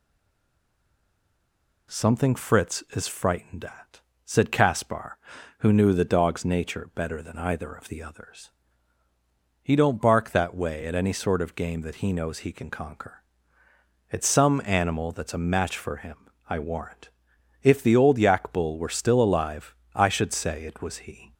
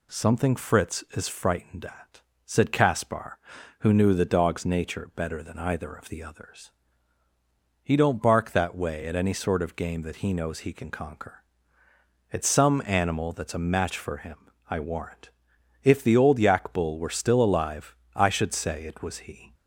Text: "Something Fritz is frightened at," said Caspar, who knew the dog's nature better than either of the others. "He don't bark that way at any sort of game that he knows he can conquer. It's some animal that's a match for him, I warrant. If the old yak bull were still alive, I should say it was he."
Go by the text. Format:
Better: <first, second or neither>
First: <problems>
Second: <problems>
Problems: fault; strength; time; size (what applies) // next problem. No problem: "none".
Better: second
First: stays silent before the first word; noticeable; until 1.9 s; 1.9 s long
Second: none